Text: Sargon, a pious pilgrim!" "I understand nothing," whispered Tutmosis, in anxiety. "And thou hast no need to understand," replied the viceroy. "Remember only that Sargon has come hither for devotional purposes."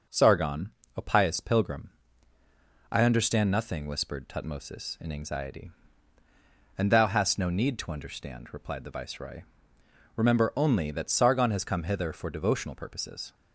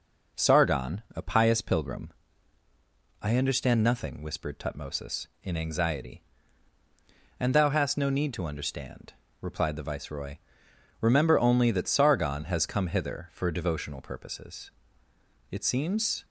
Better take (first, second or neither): first